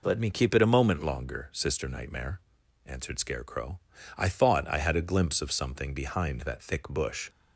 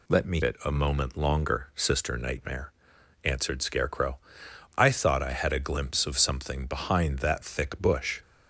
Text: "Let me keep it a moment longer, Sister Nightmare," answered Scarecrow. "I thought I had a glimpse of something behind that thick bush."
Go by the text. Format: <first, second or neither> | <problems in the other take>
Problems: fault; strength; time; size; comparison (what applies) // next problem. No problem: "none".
first | skips "keep"; at 0.4 s